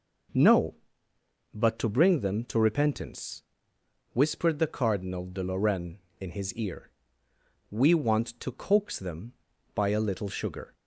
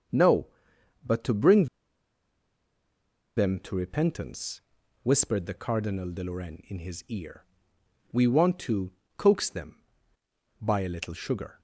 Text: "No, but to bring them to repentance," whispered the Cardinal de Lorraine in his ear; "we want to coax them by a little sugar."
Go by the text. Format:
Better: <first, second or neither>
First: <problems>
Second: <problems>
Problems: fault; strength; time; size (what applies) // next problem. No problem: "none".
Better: first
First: none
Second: starts louder than the rest; until 3.4 s; 7 dB // pauses between "bring" and "them"; strong; at 1.6 s; 1.7 s long // pauses between "to" and "coax"; slight; at 8.8 s; 0.26 s long